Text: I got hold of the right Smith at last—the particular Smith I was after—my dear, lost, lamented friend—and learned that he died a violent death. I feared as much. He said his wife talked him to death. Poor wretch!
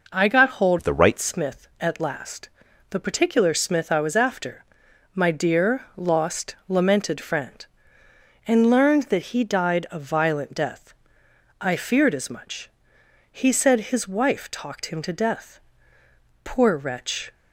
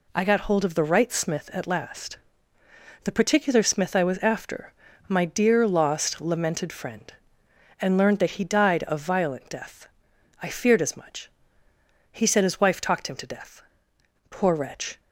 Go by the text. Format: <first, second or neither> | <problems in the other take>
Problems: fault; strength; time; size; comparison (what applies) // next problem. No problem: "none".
second | changes voice from "of" to "right"; from 0.7 to 1.1 s; 0.4 s long